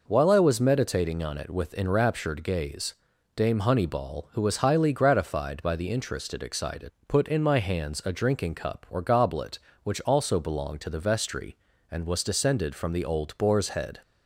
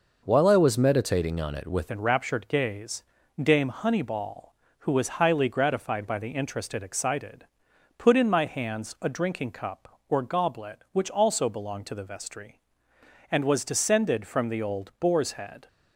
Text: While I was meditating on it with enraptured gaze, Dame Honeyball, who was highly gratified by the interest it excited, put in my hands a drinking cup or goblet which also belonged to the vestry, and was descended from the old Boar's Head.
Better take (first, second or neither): first